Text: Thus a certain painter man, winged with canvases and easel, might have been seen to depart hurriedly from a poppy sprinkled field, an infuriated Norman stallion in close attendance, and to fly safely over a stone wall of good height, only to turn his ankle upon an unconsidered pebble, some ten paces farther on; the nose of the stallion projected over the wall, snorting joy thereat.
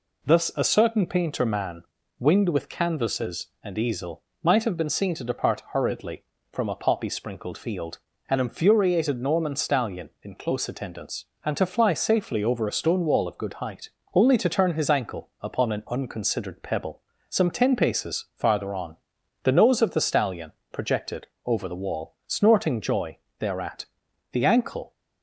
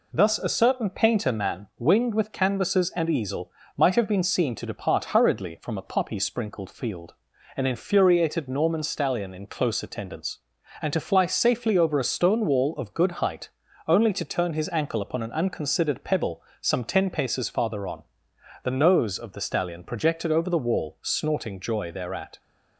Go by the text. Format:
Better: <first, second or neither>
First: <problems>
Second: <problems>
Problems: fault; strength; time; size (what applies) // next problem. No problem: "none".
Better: second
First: pauses between "stallion" and "projected"; slight; at 20.5 s; 0.18 s long // pauses between "projected" and "over"; slight; at 21.2 s; 0.20 s long // pauses between "joy" and "thereat"; slight; at 23.1 s; 0.22 s long // goes on to say "The ankle"; noticeable; from 24.3 s on; 0.62 s long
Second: none